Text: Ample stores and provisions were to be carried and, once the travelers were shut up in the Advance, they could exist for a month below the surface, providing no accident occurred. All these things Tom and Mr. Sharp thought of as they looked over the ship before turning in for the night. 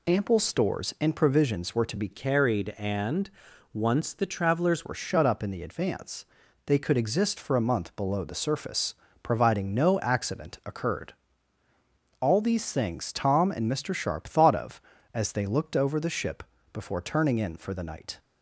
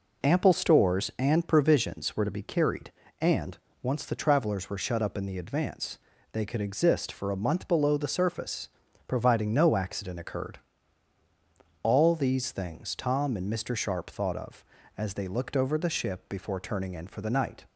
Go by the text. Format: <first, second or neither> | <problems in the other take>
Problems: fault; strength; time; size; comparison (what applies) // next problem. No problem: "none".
second | changes voice from "carried" to "travelers"; from 2.1 to 4.8 s; 2.7 s long // pauses between "ship" and "before"; slight; at 16.4 s; 0.30 s long